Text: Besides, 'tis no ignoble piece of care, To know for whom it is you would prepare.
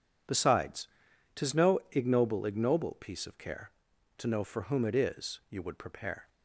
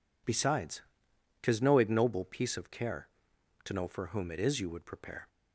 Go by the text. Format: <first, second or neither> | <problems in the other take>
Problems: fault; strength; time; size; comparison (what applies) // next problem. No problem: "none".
second | says "ignoble" twice; at 2.4 s